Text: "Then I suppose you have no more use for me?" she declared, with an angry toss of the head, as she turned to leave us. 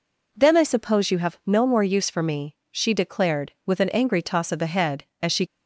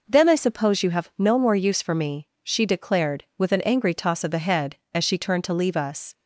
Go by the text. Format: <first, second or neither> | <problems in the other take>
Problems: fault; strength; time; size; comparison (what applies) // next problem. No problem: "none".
second | stops before "turned to leave us"; at 5.4 s